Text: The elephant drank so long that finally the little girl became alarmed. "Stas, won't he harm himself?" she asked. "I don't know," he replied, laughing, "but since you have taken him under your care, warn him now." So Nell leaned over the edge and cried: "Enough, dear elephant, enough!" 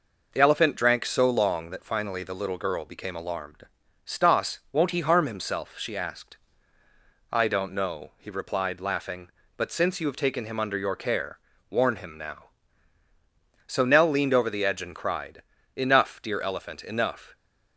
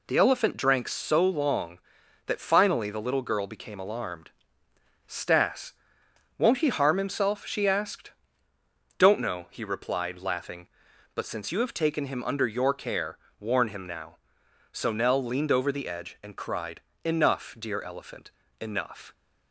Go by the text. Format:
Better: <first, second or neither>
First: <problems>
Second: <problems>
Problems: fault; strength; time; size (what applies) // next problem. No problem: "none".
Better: first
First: none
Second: skips "I"; at 8.5 s